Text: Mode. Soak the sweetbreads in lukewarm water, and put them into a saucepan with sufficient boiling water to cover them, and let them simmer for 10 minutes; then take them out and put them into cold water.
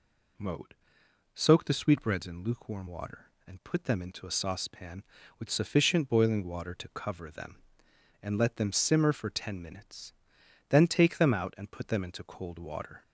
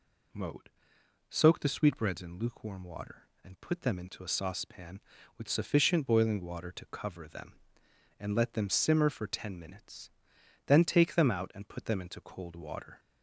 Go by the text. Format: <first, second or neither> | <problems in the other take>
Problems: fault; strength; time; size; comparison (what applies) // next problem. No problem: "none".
neither | none